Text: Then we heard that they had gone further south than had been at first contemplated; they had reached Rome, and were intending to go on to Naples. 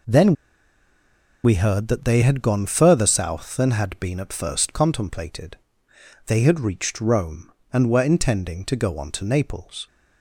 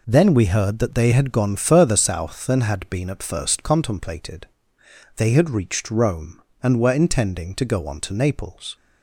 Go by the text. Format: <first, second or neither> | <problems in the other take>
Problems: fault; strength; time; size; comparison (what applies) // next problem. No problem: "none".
second | pauses between "Then" and "we"; at 0.3 s; 1.0 s long